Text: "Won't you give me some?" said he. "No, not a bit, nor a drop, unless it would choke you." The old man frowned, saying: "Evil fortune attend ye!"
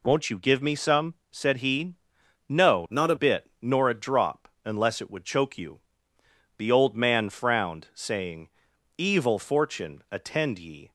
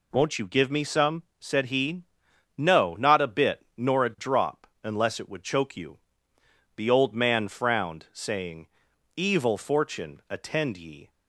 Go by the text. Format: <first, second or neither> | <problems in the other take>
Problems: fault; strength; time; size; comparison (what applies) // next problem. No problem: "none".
second | changes voice from "not" to "a"; from 2.8 to 3.1 s; 0.3 s long